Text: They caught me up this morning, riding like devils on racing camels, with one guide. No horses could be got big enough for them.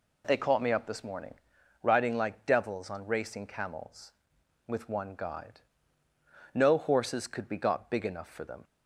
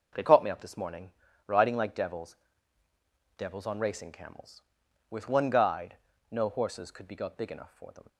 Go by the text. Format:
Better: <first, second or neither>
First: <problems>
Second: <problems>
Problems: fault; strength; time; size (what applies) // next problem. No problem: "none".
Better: first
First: none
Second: says "devils" twice; at 3.3 s